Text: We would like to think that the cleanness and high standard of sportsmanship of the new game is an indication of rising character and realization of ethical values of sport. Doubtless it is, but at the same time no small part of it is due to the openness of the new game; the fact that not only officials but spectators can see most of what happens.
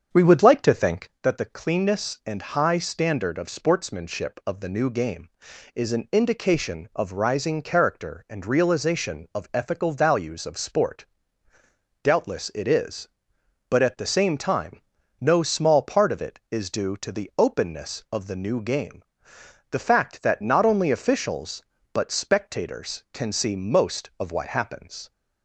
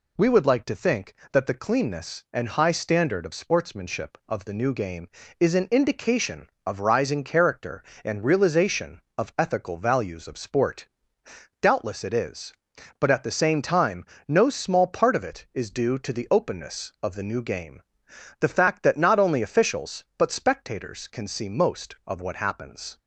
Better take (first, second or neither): second